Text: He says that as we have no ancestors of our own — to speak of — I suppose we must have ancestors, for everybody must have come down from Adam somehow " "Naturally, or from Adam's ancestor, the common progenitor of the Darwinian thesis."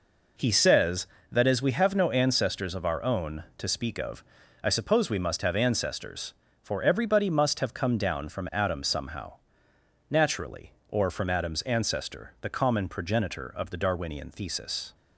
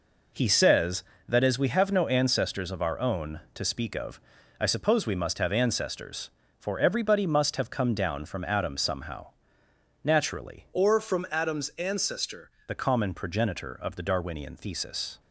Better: first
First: none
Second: changes voice from "or" to "ancestor"; from 10.7 to 12.5 s; 1.8 s long

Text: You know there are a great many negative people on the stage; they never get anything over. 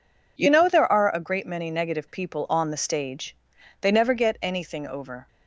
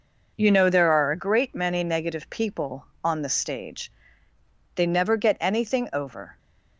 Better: neither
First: none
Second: none

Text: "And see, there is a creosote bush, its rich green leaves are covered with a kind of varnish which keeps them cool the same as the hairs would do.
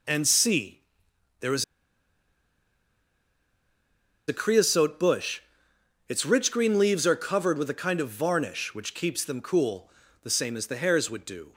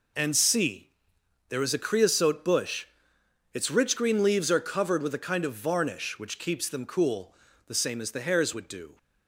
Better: second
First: pauses between "is" and "a"; strong; at 1.6 s; 2.6 s long // pauses between "cool" and "the"; slight; at 9.8 s; 0.34 s long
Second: pauses between "cool" and "the"; slight; at 7.3 s; 0.34 s long

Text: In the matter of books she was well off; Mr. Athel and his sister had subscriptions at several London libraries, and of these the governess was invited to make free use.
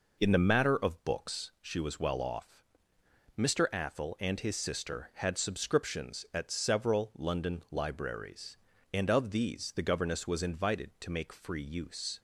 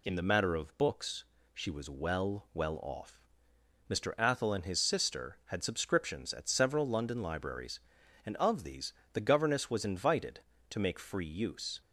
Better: first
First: none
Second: pauses between "books" and "she"; slight; at 1.2 s; 0.30 s long // says "well" twice; at 2.5 s // pauses between "these" and "the"; slight; at 8.9 s; 0.22 s long

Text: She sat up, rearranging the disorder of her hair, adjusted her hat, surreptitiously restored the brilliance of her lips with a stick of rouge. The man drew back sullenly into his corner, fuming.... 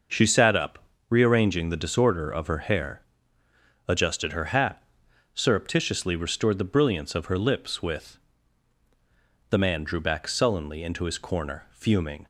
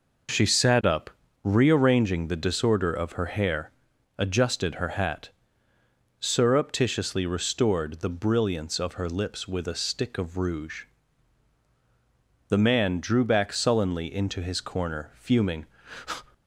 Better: second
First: starts louder than the rest; noticeable; until 1.4 s; 6 dB // skips "a stick of rouge"; at 8.8 s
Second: none

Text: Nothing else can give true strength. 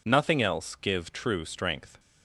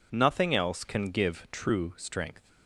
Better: second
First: skips "can"; at 0.7 s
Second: none

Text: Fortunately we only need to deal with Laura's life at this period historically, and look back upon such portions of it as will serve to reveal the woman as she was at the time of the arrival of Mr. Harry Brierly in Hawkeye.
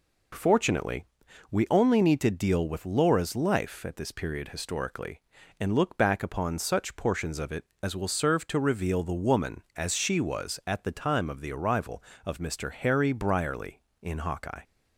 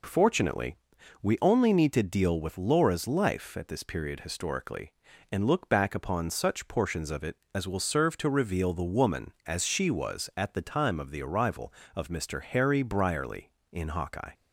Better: neither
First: pauses between "Fortunately" and "we"; at 1.0 s; 0.44 s long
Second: pauses between "Fortunately" and "we"; at 0.7 s; 0.44 s long

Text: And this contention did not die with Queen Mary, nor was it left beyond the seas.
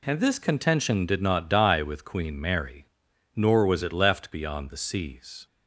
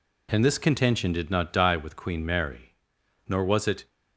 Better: first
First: none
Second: stops before "left beyond the seas"; at 3.8 s

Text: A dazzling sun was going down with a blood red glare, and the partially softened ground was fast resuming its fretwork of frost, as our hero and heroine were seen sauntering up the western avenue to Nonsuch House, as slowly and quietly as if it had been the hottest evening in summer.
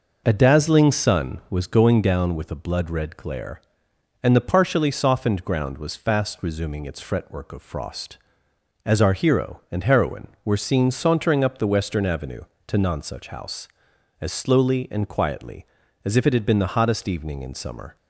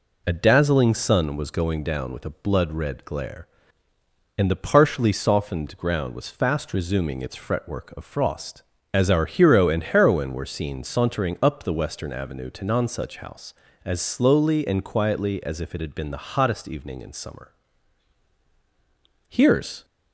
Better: first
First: none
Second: goes on to say "Here's"; from 19.2 s on; 0.56 s long

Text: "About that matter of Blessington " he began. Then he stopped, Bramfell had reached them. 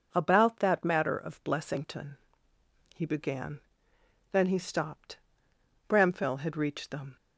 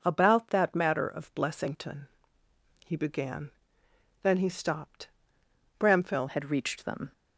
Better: first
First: none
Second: changes voice at "had"; from 6.2 s on; 0.9 s long

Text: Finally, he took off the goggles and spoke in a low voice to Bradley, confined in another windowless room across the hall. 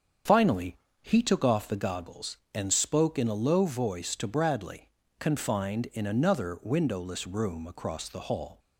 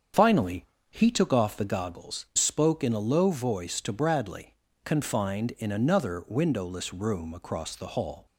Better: first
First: starts louder than the rest; strong; until 1.5 s; 7.5 dB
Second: starts louder than the rest; strong; until 1.4 s; 7.5 dB // skips "and"; at 2.3 s

